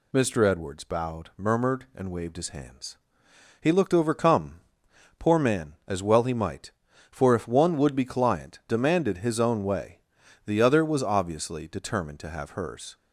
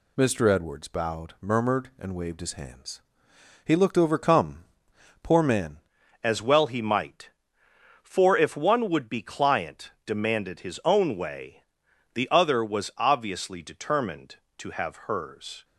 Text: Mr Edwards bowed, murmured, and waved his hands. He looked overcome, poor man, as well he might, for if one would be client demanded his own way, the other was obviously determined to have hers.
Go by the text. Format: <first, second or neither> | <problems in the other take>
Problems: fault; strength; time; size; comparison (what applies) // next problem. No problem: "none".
first | changes voice at "as"; from 6.2 s on; 9.4 s long